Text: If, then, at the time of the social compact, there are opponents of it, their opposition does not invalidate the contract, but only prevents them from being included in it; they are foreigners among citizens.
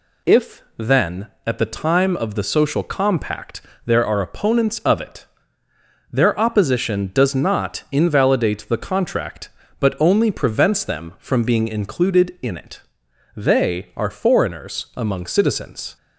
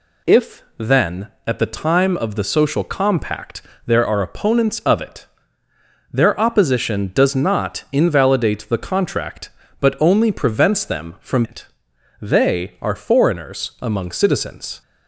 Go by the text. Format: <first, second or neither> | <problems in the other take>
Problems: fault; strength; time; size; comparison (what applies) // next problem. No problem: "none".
first | skips "being included in"; at 11.4 s